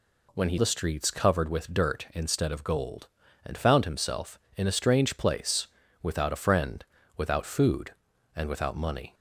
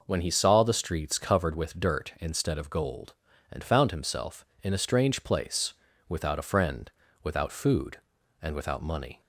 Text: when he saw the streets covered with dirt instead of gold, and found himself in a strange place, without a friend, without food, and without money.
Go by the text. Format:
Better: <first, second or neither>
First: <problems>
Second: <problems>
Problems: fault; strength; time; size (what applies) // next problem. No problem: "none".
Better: second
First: skips "saw"; at 0.5 s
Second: none